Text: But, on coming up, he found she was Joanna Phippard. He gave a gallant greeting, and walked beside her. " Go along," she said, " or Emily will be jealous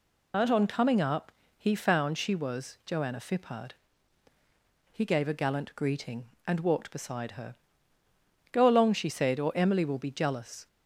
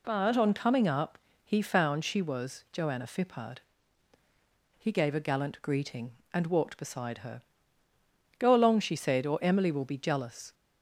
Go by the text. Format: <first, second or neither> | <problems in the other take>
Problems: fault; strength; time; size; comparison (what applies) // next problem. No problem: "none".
second | loses the start of "But"; at 0.3 s; 165 ms